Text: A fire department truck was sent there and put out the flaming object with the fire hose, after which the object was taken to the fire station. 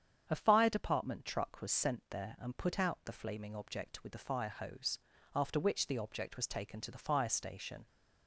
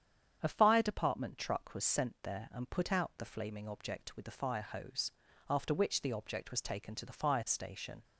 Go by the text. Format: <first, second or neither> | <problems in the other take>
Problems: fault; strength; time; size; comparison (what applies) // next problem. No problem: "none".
neither | starts louder than the rest; strong; the same in both